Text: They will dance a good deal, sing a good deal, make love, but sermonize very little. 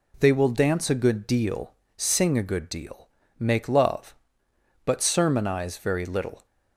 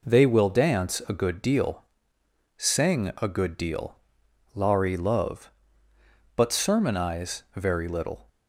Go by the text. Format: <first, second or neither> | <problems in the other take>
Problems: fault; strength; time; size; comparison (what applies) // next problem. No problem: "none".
first | says "lari" for "make"; at 4.5 s